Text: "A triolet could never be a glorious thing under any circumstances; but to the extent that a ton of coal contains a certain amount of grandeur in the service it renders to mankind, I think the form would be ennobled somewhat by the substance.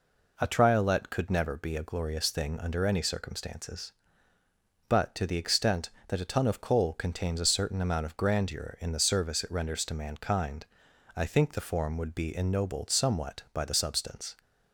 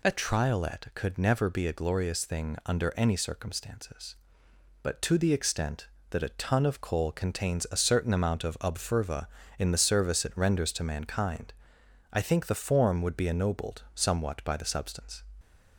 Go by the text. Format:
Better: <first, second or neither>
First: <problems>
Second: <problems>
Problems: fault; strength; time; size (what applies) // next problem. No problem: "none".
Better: first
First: none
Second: says "obferva" for "grandeur"; at 8.5 s